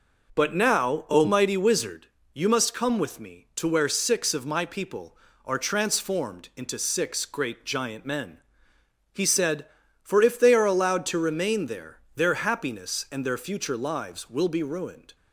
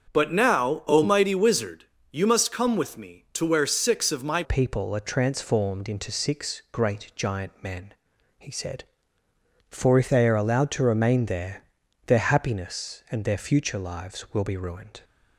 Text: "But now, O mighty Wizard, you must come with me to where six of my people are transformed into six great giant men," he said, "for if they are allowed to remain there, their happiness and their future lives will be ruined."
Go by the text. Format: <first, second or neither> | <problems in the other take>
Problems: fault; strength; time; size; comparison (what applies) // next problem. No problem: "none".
first | starts louder than the rest; until 1.1 s; 6.5 dB // changes voice at "people"; from 4.4 s on; 10.6 s long